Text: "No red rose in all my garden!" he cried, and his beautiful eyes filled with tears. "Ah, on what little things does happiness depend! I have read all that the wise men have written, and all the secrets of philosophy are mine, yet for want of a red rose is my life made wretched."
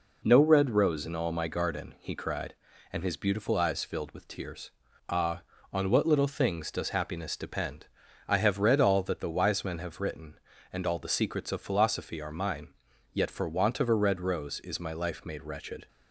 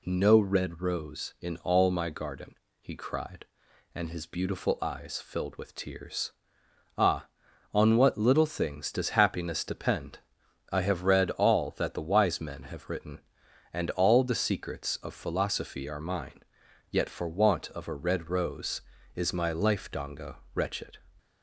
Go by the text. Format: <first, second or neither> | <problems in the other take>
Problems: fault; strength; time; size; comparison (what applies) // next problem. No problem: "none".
first | says "donga" for "made"; at 19.9 s